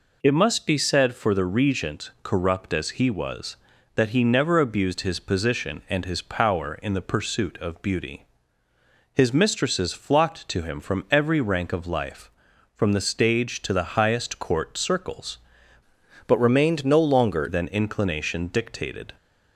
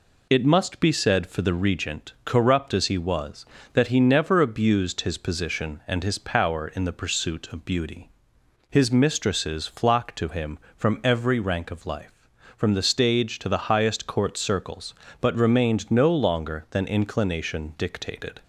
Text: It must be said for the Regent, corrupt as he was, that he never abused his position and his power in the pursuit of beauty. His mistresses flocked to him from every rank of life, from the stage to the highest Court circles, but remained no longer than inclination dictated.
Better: second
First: changes voice from "but" to "longer"; from 16.2 to 17.4 s; 1.2 s long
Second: none

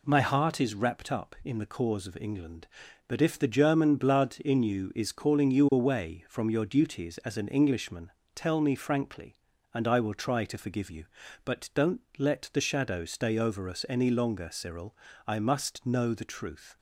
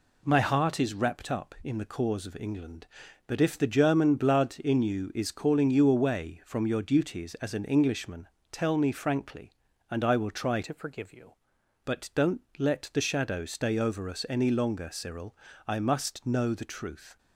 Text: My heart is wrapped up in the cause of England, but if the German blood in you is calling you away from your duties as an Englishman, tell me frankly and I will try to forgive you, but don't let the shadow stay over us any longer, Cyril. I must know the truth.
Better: first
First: pauses between "don't" and "let"; slight; at 11.9 s; 0.18 s long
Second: changes voice from "to" to "you"; from 10.6 to 11.3 s; 0.7 s long // pauses between "don't" and "let"; slight; at 12.3 s; 0.18 s long

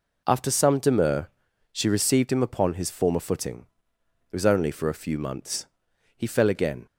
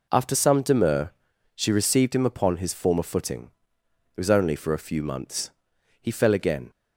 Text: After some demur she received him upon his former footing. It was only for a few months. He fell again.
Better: neither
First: pauses between "demur" and "she"; noticeable; at 1.2 s; 0.46 s long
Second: pauses between "demur" and "she"; noticeable; at 1.1 s; 0.46 s long

